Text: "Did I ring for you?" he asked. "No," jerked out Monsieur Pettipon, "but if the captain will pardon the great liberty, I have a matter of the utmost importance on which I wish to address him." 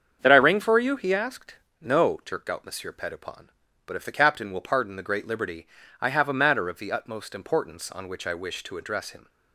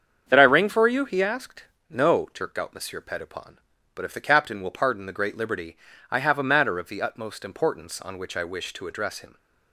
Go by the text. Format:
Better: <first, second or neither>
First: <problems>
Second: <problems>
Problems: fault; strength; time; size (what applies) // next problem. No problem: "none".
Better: neither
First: starts louder than the rest; strong; until 1.2 s; 7.5 dB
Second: starts louder than the rest; strong; until 1.2 s; 7.5 dB